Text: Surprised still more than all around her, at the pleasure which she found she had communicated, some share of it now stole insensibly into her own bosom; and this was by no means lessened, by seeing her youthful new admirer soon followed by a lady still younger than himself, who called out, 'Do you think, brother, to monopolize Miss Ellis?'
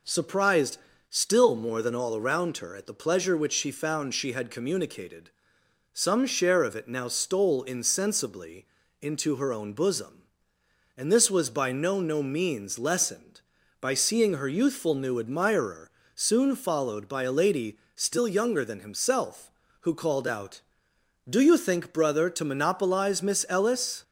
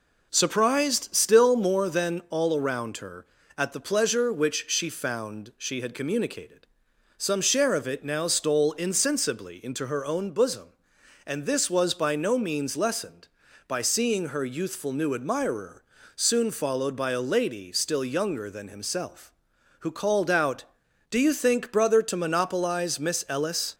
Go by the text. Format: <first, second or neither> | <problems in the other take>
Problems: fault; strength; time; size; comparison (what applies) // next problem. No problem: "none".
second | pauses between "Surprised" and "still"; slight; at 0.7 s; 0.32 s long // pauses between "insensibly" and "into"; slight; at 8.6 s; 0.36 s long // says "no" twice; at 12.0 s // pauses between "admirer" and "soon"; slight; at 15.8 s; 0.24 s long; slight in the second // pauses between "lady" and "still"; slight; at 17.7 s; 0.16 s long